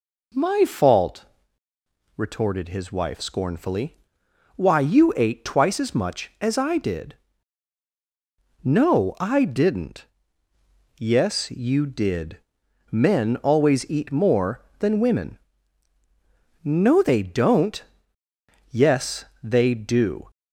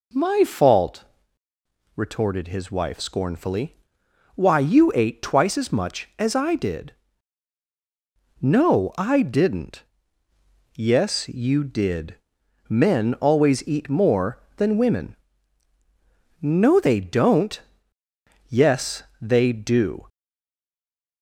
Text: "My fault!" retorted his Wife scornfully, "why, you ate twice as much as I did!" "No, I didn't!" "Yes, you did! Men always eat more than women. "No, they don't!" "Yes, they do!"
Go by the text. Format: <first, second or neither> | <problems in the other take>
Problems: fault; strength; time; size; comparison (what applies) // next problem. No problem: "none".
first | stays silent after the last word; from 20.0 s on; 1.2 s long